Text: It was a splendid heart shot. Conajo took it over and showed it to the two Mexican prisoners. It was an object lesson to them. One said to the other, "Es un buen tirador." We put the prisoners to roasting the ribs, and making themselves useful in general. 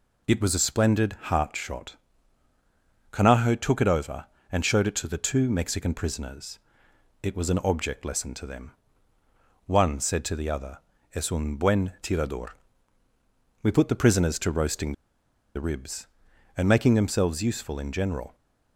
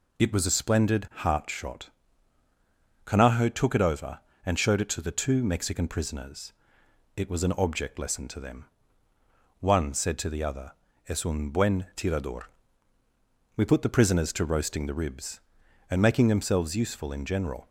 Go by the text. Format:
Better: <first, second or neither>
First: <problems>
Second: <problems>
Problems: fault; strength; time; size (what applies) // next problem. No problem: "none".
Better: second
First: pauses between "roasting" and "the"; noticeable; at 14.9 s; 0.61 s long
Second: none